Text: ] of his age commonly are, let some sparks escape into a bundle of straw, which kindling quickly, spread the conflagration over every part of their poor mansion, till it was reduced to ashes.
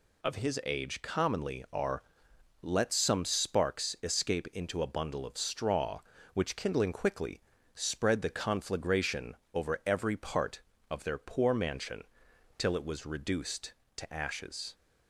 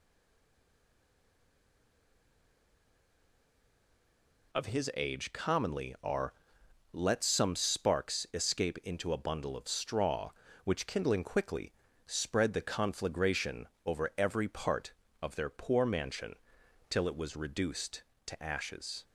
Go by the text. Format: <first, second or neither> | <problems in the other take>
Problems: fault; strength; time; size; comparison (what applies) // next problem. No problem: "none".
first | stays silent before the first word; strong; until 4.5 s; 4.5 s long // pauses between "conflagration" and "over"; slight; at 13.6 s; 0.18 s long; slight in the first